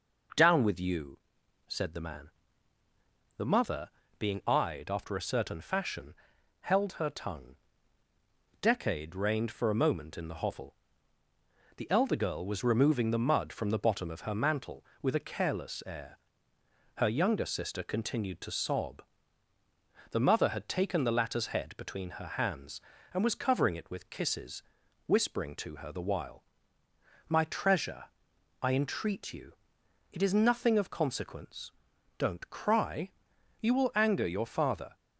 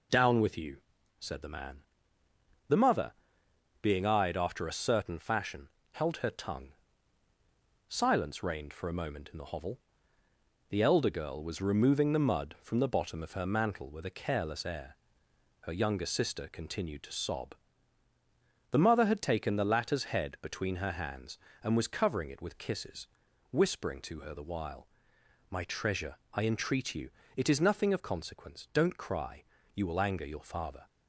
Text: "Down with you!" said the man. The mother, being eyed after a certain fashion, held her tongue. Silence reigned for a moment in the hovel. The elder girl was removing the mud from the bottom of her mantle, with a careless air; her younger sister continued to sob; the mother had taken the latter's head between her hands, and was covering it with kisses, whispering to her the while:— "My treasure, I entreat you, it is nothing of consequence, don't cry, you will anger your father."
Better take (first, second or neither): second